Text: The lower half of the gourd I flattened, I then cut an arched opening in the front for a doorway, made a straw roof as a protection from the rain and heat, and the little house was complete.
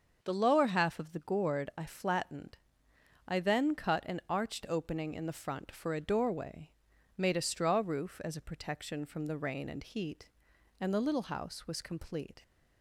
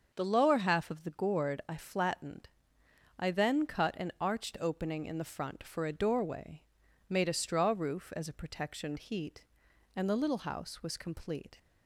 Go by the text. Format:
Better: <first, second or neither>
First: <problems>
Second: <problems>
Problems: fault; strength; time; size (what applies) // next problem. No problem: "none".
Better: first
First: starts louder than the rest; until 1.2 s; 6.5 dB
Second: starts louder than the rest; until 1.1 s; 6.5 dB // skips "from the rain and"; at 8.9 s